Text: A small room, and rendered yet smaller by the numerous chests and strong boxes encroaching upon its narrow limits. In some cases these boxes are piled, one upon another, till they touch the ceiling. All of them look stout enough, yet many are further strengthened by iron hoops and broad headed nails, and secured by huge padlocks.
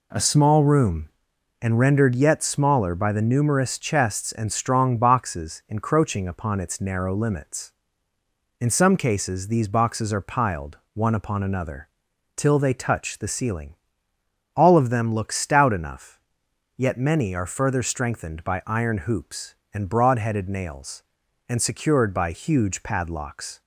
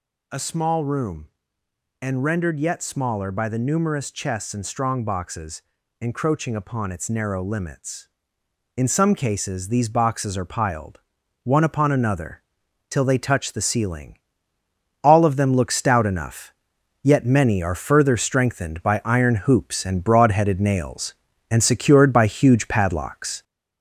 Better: first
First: none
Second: gets louder; noticeable; throughout; 4 dB // pauses between "boxes" and "encroaching"; at 5.6 s; 0.40 s long

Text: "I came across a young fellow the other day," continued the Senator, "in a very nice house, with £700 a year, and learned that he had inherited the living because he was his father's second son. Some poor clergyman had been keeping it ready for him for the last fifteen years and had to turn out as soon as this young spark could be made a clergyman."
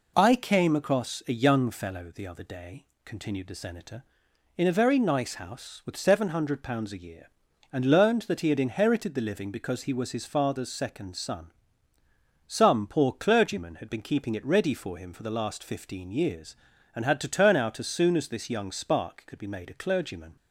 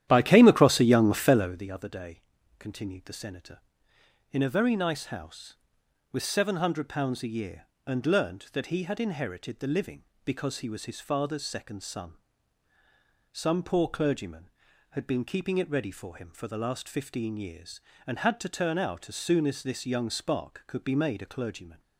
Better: first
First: none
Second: starts louder than the rest; strong; until 1.6 s; 11.5 dB

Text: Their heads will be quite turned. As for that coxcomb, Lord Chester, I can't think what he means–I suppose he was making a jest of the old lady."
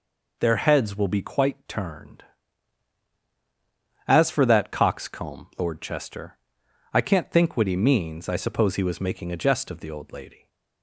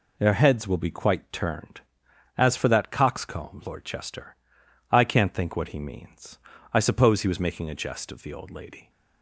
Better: neither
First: none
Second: none

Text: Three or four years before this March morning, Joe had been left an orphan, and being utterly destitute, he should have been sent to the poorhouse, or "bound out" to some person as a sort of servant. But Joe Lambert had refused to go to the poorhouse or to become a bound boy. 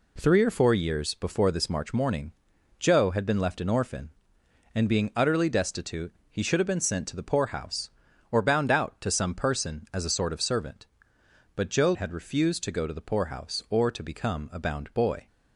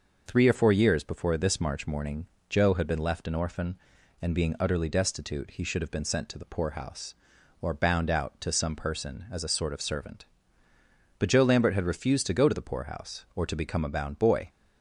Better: second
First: skips "Lambert"; at 11.9 s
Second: none

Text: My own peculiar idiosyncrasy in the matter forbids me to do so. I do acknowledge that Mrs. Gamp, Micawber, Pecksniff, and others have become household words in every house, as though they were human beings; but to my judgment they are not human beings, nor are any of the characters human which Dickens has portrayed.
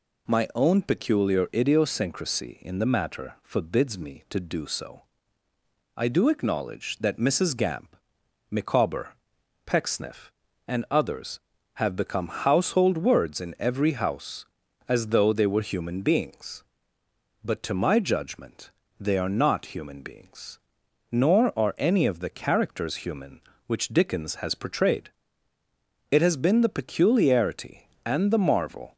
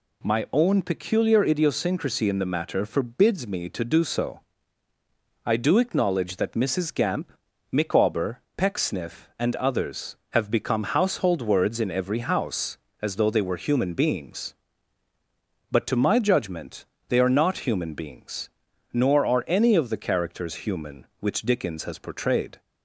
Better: second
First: pauses between "judgment" and "they"; slight; at 18.6 s; 0.30 s long // goes on to say "It has been the peculiarity and the marvel"; strong; from 26.1 s on; 2.8 s long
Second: pauses between "judgment" and "they"; slight; at 16.8 s; 0.22 s long

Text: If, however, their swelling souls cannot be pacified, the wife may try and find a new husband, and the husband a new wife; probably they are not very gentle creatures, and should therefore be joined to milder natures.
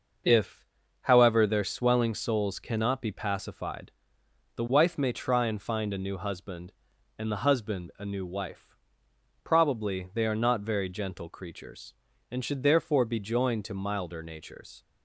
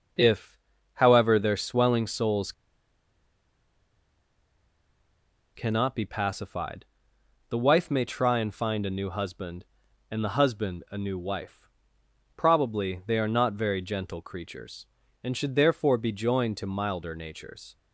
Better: first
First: none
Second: pauses between "souls" and "cannot"; strong; at 2.5 s; 3.0 s long

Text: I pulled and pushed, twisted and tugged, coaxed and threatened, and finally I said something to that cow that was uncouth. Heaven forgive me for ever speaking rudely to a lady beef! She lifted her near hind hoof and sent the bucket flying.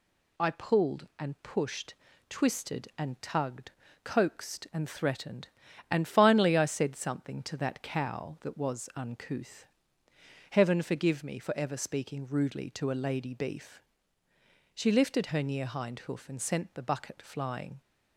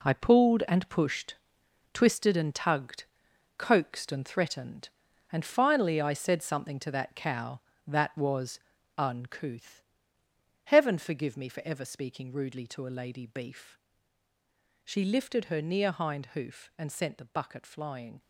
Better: first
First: none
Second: gets quieter; strong; throughout; 10.5 dB // pauses between "was" and "uncouth"; at 8.6 s; 0.38 s long

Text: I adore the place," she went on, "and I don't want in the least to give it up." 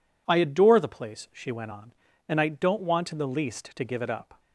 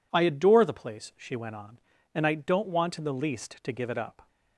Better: neither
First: none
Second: none

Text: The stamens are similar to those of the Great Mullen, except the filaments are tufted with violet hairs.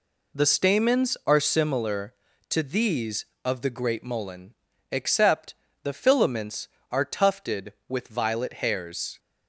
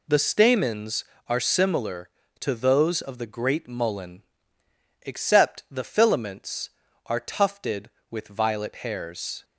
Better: second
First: says "these" for "those"; at 2.6 s // pauses between "except" and "the"; slight; at 5.5 s; 0.30 s long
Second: none

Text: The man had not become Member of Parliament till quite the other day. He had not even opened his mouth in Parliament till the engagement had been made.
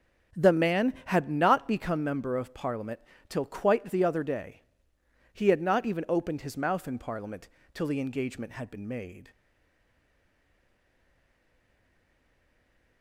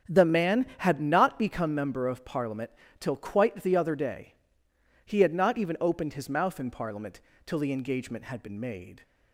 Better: second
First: starts louder than the rest; strong; until 1.4 s; 7 dB // pauses between "Parliament" and "till"; slight; at 2.9 s; 0.28 s long // pauses between "Parliament" and "till"; slight; at 7.4 s; 0.24 s long // stays silent after the last word; strong; from 9.3 s on; 3.7 s long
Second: starts louder than the rest; strong; until 1.2 s; 8 dB // pauses between "Parliament" and "till"; slight; at 2.7 s; 0.28 s long // pauses between "Parliament" and "till"; slight; at 7.2 s; 0.24 s long

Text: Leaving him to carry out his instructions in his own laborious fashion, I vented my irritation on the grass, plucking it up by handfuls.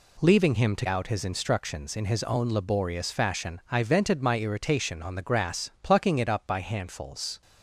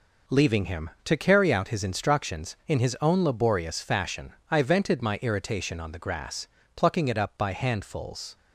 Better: second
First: skips "carry"; at 0.8 s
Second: none

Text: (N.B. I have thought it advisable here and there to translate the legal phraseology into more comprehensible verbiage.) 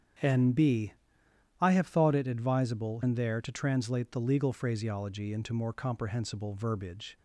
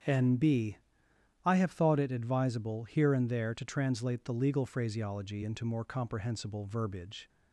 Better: second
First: starts louder than the rest; strong; until 1.8 s; 8 dB // skips "here"; at 3.0 s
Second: starts louder than the rest; strong; until 1.7 s; 7.5 dB

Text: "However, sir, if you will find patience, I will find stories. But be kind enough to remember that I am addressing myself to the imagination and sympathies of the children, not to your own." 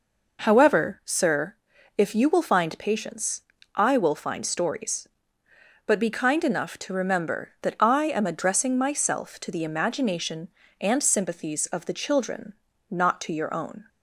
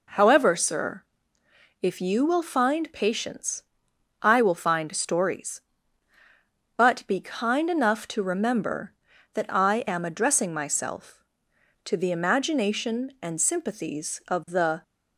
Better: first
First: none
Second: stops before "children not to your own"; at 14.8 s

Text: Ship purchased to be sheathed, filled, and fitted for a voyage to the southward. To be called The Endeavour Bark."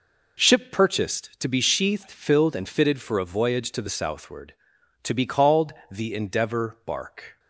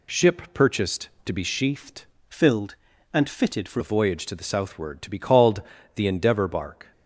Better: first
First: pauses between "called" and "The"; slight; at 5.7 s; 0.18 s long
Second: changes voice from "filled" to "for"; from 2.2 to 3.8 s; 1.6 s long // pauses between "called" and "The"; slight; at 5.6 s; 0.34 s long

